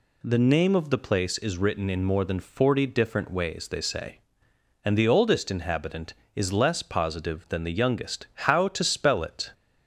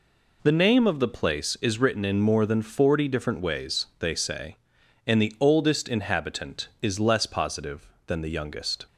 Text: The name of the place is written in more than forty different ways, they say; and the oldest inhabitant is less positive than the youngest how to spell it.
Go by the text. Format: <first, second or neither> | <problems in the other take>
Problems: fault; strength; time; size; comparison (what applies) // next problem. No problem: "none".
first | stops before "how to spell it"; at 8.8 s